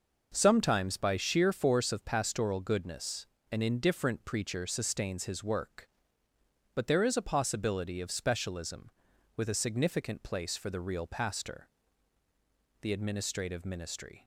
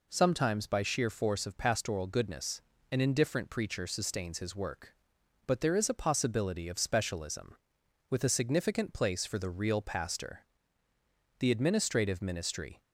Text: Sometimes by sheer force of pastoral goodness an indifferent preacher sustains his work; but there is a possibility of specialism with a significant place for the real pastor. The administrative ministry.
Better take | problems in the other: neither | pauses between "goodness" and "an"; slight; the same in both

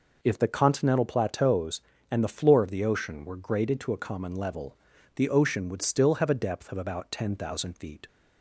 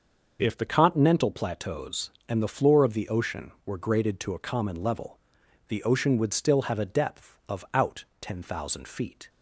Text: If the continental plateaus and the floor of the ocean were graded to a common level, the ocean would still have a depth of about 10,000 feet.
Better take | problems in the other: first | starts louder than the rest; until 1.4 s; 6 dB // says "out" for "about"; at 7.7 s

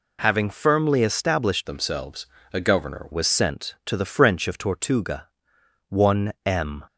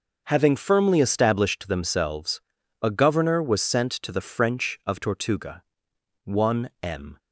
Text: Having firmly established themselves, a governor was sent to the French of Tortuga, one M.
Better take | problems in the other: second | changes voice from "themselves" to "governor"; from 1.6 to 3.0 s; 1.4 s long

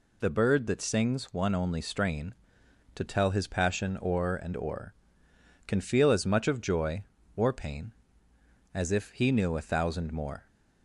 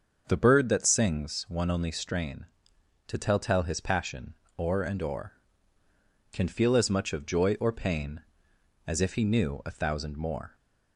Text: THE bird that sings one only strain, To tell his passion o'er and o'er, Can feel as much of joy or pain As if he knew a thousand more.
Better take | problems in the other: first | starts louder than the rest; until 1.2 s; 6.5 dB // says "tell" twice; at 3.3 s // pauses between "passion" and "o'er"; slight; at 4.3 s; 0.24 s long

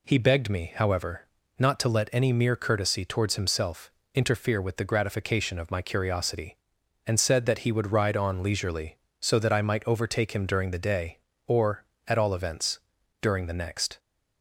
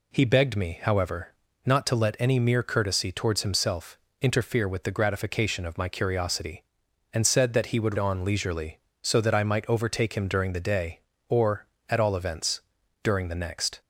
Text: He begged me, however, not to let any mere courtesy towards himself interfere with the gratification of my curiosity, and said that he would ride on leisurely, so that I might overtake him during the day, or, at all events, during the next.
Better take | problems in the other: first | pauses between "himself" and "interfere"; slight; at 3.9 s; 0.22 s long; slight in the first // skips "ride"; at 7.9 s

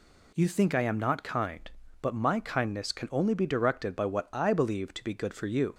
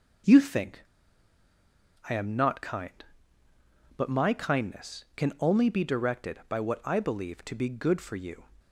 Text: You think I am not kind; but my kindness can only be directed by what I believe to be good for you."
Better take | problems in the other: first | starts louder than the rest; until 2.5 s; 6.5 dB // pauses between "think" and "I"; at 0.8 s; 1.2 s long

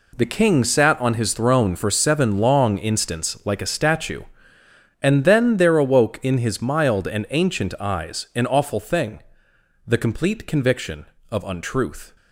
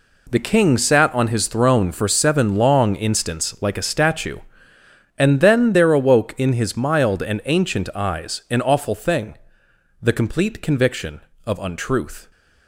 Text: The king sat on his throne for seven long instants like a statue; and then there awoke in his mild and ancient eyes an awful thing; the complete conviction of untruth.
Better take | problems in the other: neither | none

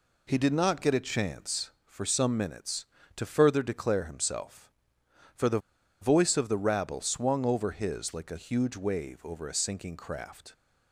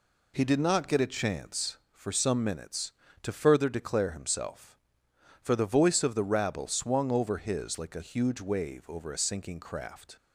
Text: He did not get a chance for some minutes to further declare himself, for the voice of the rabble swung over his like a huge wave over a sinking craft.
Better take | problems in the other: second | pauses between "the" and "voice"; at 5.5 s; 0.43 s long

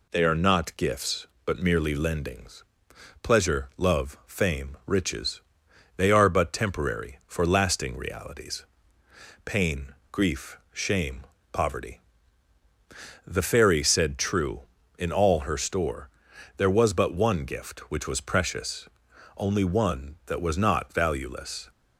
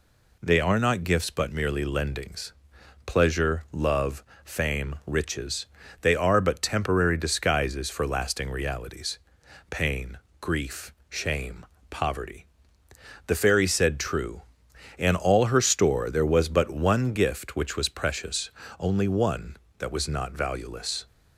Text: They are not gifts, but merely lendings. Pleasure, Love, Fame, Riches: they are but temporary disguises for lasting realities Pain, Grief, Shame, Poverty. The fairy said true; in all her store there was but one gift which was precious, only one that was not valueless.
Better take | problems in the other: second | skips "disguises"; at 7.2 s // pauses between "realities" and "Pain"; noticeable; at 8.6 s; 0.80 s long; noticeable in the second // pauses between "store" and "there"; noticeable; at 16.0 s; 0.48 s long

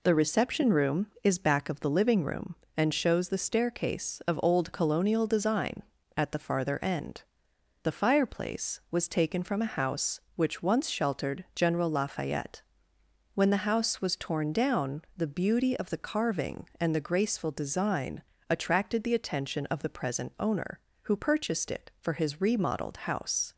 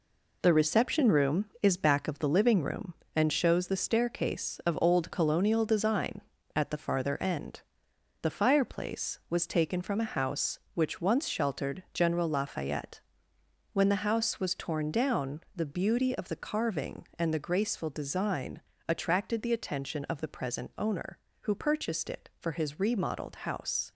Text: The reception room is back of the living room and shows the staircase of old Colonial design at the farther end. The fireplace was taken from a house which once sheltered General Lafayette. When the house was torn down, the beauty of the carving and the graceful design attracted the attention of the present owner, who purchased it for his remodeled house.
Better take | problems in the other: first | gets quieter; throughout; 7 dB // pauses between "design" and "attracted"; slight; at 18.6 s; 0.26 s long; slight in the first

